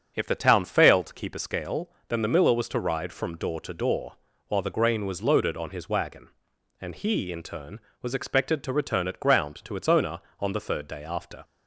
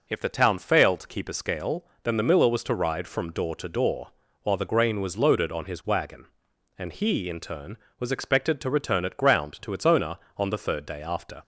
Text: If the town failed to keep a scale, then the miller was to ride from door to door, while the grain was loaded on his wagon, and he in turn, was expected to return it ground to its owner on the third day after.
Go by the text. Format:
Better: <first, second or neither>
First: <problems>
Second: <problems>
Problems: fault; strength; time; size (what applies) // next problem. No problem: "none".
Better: second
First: starts louder than the rest; until 1.1 s; 7 dB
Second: none